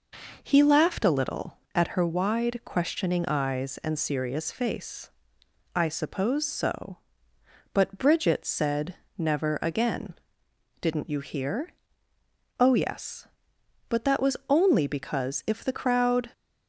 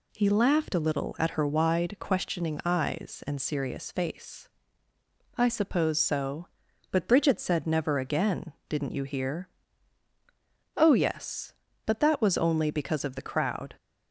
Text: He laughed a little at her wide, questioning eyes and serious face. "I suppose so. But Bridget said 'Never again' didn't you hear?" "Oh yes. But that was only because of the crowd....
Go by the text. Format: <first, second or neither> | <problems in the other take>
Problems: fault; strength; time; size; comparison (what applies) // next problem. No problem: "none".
second | pauses between "said" and "Never"; slight; at 8.9 s; 0.22 s long // pauses between "again" and "didn't"; noticeable; at 10.1 s; 0.66 s long; slight in the second // says "if" for "of"; at 15.4 s